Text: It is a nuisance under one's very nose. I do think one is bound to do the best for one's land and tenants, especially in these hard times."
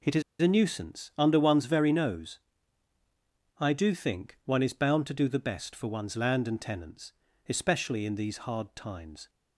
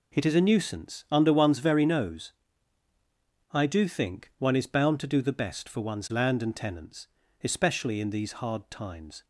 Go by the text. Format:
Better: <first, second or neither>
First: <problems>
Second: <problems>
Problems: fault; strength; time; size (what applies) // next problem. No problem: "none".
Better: second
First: pauses between "is" and "a"; slight; at 0.2 s; 0.18 s long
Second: none